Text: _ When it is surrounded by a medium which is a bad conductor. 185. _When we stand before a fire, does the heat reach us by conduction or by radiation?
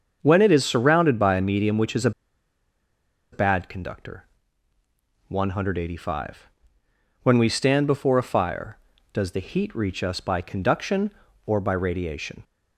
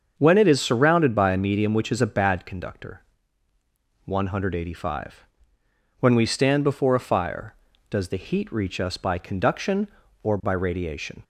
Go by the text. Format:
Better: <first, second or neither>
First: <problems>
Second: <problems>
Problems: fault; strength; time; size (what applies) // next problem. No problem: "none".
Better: second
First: starts louder than the rest; until 1.2 s; 7 dB // pauses between "a" and "bad"; at 2.1 s; 1.2 s long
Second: starts louder than the rest; until 1.1 s; 7 dB